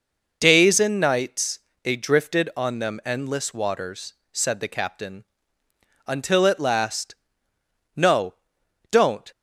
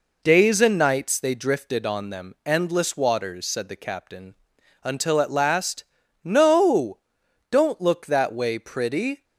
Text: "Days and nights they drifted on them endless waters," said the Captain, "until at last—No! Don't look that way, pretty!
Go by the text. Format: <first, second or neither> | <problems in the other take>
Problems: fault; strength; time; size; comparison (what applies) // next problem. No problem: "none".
second | pauses between "nights" and "they"; slight; at 1.5 s; 0.24 s long // stops before "look that way pretty"; at 9.3 s